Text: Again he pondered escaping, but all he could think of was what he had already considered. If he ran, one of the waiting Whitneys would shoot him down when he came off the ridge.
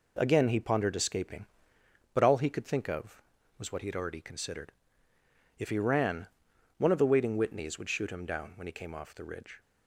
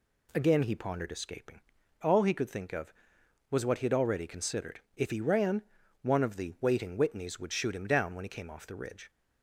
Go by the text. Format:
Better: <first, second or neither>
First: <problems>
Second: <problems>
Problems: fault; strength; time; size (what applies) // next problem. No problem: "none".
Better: first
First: none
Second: skips "but"; at 1.8 s